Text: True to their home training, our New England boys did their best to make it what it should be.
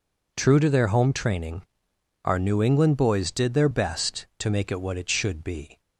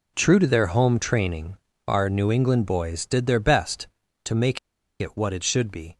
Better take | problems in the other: first | pauses between "make" and "it"; at 4.5 s; 0.42 s long

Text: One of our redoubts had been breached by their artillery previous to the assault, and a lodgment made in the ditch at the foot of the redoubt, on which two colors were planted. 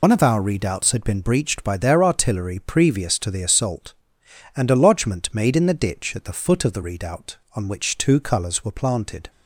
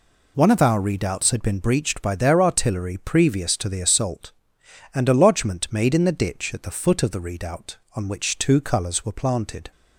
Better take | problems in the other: second | loses the start of "One"; at 0.0 s; 65 ms

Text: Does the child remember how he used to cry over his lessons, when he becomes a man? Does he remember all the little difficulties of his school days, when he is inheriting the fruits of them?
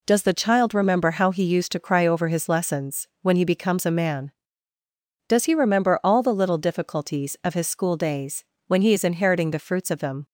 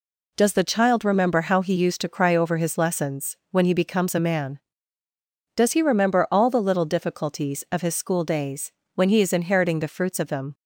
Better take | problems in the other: neither | none

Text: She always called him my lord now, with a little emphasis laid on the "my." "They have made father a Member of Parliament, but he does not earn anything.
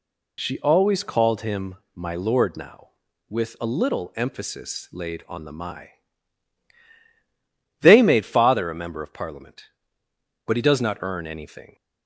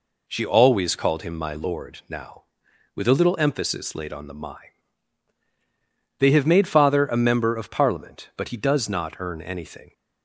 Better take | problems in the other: second | pauses between "him" and "my"; slight; at 1.7 s; 0.22 s long // skips "have"; at 8.0 s

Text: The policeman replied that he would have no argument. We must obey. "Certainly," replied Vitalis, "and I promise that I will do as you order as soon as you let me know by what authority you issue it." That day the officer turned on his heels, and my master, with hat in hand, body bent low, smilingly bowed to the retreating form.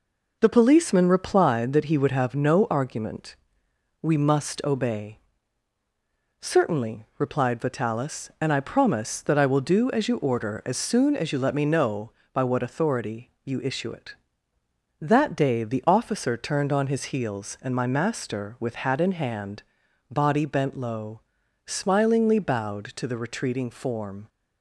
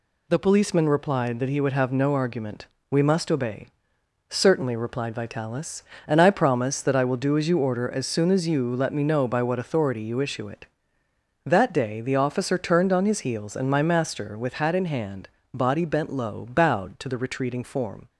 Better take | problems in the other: first | skips "smilingly"; at 16.4 s

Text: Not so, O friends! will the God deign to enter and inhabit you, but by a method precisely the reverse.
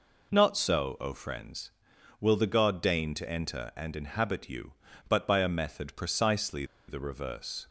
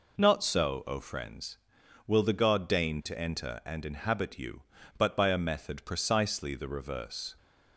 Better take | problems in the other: second | pauses between "precisely" and "the"; slight; at 6.6 s; 0.22 s long

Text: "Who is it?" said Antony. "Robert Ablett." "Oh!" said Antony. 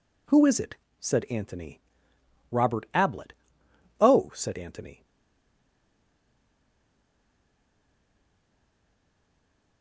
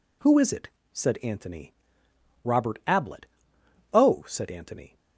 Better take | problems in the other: second | stays silent after the last word; strong; from 5.0 s on; 4.8 s long

